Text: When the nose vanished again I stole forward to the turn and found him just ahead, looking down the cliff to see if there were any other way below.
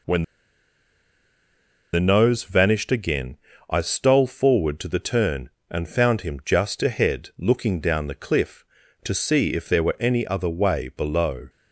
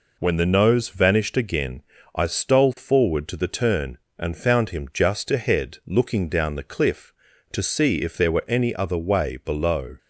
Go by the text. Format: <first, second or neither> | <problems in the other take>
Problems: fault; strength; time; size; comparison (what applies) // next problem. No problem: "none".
second | pauses between "When" and "the"; strong; at 0.2 s; 1.7 s long // pauses between "again" and "I"; slight; at 3.3 s; 0.34 s long; slight in the second